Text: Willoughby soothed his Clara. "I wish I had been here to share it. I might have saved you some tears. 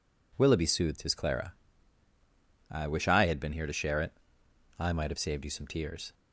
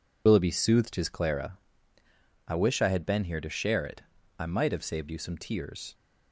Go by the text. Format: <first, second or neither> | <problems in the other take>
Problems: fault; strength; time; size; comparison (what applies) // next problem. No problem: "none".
first | loses the start of "Willoughby"; at 0.2 s; 60 ms